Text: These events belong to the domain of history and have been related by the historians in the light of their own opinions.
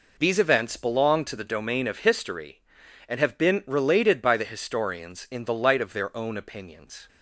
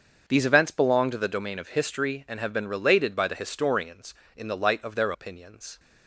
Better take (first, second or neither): first